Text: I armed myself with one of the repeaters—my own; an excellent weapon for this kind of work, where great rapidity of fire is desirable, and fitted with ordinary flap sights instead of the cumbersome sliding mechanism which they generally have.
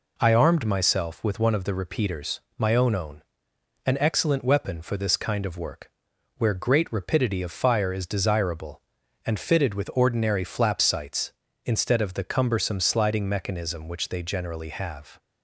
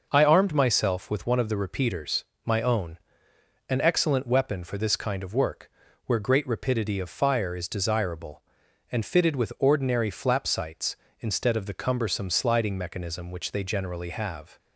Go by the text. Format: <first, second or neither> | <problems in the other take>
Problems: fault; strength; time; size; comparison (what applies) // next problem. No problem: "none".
second | says "own" twice; at 2.9 s